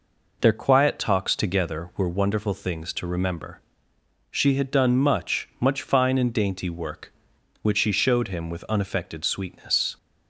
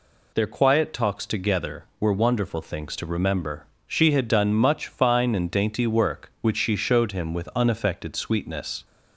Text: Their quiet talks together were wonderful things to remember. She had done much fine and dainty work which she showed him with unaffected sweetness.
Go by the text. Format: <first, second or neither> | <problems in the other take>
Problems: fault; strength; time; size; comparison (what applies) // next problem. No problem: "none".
second | says "much" twice; at 5.5 s